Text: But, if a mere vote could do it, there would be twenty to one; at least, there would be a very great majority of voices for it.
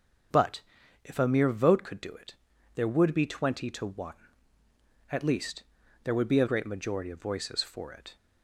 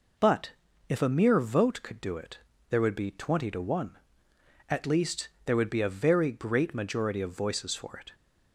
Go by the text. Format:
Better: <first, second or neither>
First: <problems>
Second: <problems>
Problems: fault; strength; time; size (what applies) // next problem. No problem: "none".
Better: second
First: starts louder than the rest; until 1.7 s; 7 dB // skips "very"; at 6.4 s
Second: none